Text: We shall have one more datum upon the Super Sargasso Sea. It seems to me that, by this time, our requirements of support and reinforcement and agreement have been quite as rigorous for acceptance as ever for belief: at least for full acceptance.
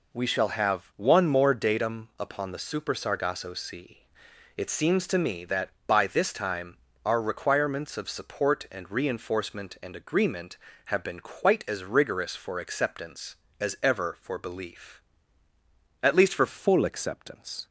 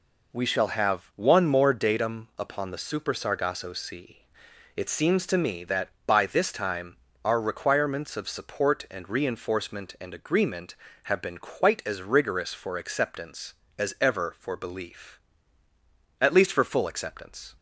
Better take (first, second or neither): second